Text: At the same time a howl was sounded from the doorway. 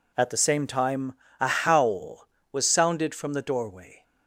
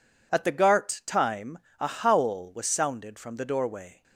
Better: first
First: pauses between "time" and "a"; slight; at 1.1 s; 0.26 s long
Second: says "gart" for "same"; at 0.5 s // pauses between "time" and "a"; slight; at 1.5 s; 0.22 s long

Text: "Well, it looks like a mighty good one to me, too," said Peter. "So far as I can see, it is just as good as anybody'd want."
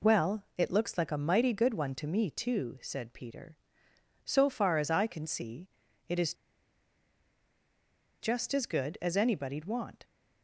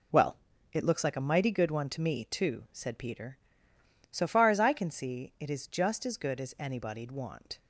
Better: second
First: pauses between "is" and "just"; strong; at 6.3 s; 1.8 s long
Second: none

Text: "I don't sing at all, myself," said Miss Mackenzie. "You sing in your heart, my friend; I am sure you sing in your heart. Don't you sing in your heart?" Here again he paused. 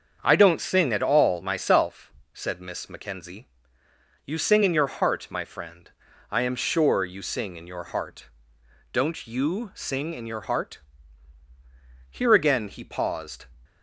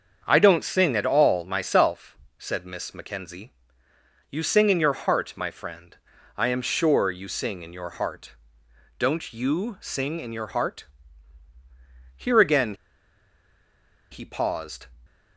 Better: first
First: starts louder than the rest; until 1.2 s; 7 dB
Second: starts louder than the rest; until 1.2 s; 7 dB // pauses between "again" and "he"; strong; at 12.7 s; 1.3 s long

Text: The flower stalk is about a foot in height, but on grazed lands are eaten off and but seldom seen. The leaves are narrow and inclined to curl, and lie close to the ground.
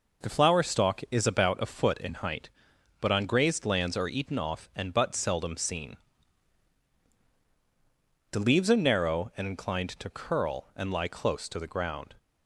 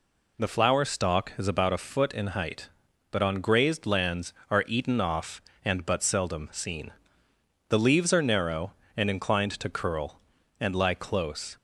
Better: first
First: none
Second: stops before "to the ground"; at 11.5 s

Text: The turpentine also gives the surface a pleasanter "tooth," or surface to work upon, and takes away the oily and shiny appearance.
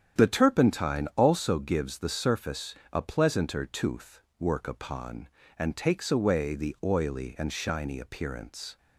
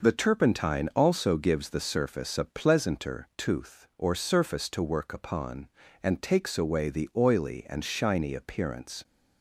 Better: second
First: starts louder than the rest; strong; until 1.2 s; 8.5 dB // pauses between "surface" and "a"; slight; at 2.7 s; 0.18 s long // skips "or surface to"; at 4.2 s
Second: none

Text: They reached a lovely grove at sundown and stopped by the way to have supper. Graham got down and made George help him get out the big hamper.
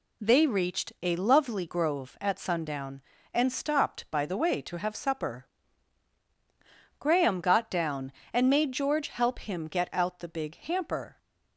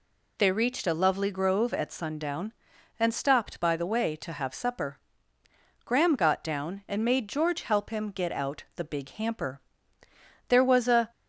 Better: first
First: none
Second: goes on to say "There was a"; noticeable; from 10.4 s on; 0.62 s long

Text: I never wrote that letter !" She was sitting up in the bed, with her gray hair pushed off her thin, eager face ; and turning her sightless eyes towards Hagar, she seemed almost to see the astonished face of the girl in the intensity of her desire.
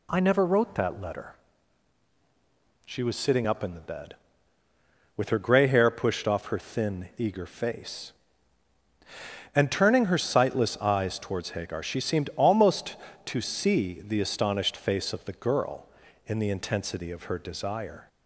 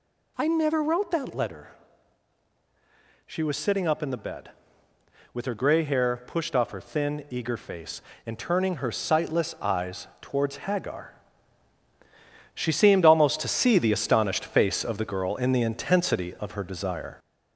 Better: first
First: none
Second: gets louder; strong; throughout; 11 dB

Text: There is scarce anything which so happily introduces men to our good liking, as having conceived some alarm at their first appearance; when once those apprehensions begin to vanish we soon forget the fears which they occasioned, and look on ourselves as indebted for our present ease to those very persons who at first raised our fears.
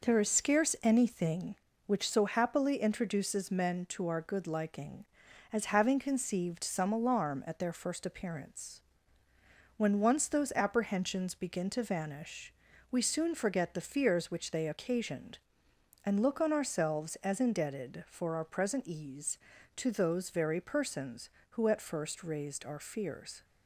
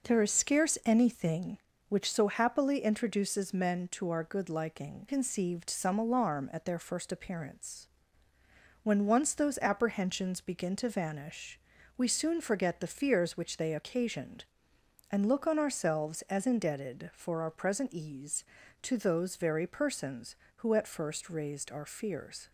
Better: first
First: pauses between "vanish" and "we"; at 12.5 s; 0.38 s long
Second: skips "as having"; at 5.0 s // pauses between "vanish" and "we"; at 11.5 s; 0.38 s long

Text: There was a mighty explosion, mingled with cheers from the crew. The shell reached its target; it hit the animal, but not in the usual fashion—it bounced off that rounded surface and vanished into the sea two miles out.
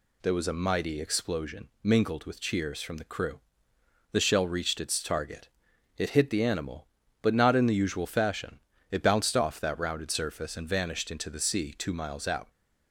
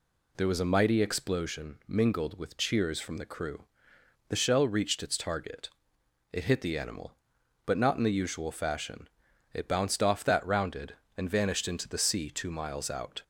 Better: first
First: none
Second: skips "surface"; at 11.0 s

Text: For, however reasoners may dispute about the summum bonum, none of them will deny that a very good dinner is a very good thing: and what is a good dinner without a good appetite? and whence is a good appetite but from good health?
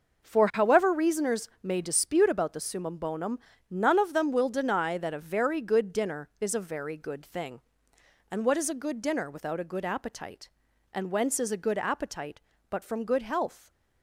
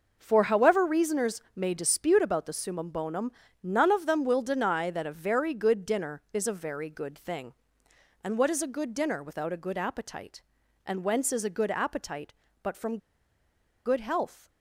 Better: first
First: none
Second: pauses between "from" and "good"; noticeable; at 12.9 s; 0.87 s long

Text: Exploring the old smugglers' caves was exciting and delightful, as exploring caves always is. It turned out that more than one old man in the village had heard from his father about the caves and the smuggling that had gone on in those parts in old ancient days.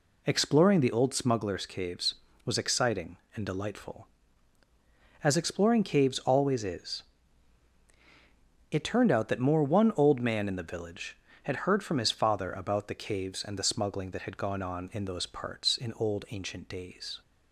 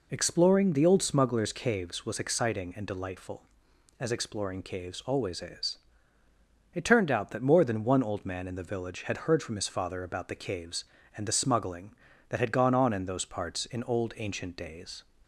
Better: second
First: skips "than"; at 9.6 s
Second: none

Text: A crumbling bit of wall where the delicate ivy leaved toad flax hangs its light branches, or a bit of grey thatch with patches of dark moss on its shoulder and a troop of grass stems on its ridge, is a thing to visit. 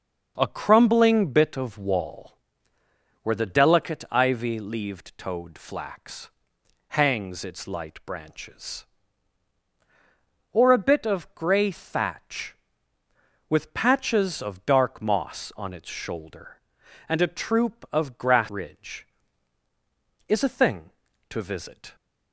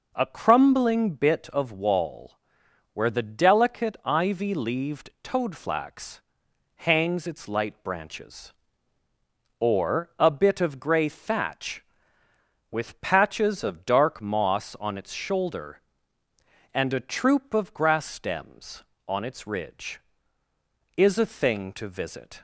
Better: second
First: starts louder than the rest; until 1.3 s; 6.5 dB // pauses between "wall" and "where"; noticeable; at 2.3 s; 0.86 s long // pauses between "flax" and "hangs"; noticeable; at 6.3 s; 0.58 s long // skips "stems on its"; at 18.4 s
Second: pauses between "wall" and "where"; noticeable; at 2.3 s; 0.56 s long // pauses between "flax" and "hangs"; noticeable; at 6.2 s; 0.56 s long

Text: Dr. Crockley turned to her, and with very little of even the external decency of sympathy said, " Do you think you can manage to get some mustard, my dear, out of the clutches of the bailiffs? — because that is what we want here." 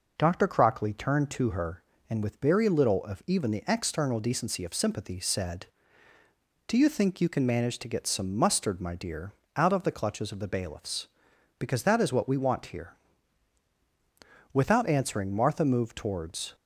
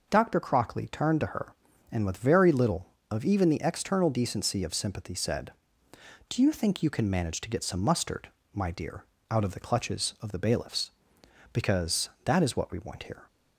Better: second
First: starts louder than the rest; noticeable; until 1.1 s; 6 dB // goes on to say "Without answering Martha moved towards"; strong; from 14.5 s on; 2.0 s long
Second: starts louder than the rest; until 1.1 s; 6 dB

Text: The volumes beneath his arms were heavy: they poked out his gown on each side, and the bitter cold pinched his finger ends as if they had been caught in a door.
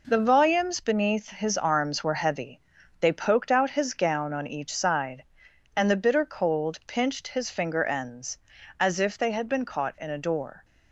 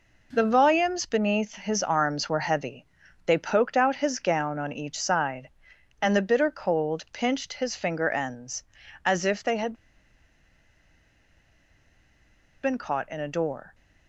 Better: first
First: none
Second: pauses between "had" and "been"; strong; at 9.7 s; 2.9 s long

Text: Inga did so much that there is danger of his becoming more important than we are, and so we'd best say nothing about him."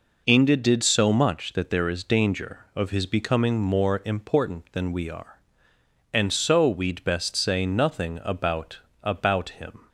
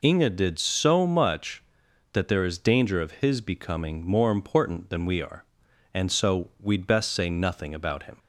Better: second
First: says "about" twice; at 9.0 s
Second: none

